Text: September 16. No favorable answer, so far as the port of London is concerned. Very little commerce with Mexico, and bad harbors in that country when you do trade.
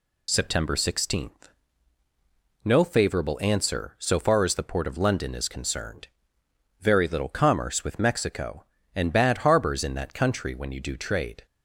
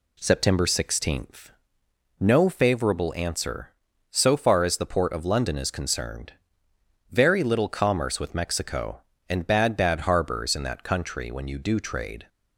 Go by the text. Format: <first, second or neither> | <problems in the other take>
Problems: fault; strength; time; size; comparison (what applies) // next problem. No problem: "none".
first | says "bad" twice; at 9.7 s